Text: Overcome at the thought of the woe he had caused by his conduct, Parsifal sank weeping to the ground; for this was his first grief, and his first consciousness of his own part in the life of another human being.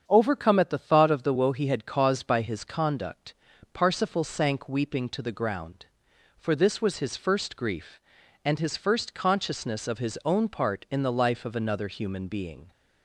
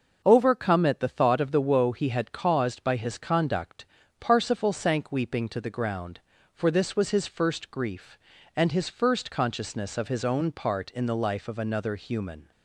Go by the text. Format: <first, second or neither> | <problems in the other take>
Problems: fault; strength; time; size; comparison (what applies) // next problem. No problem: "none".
first | starts louder than the rest; until 1.2 s; 6 dB; strong in the first // stops before "being"; at 12.5 s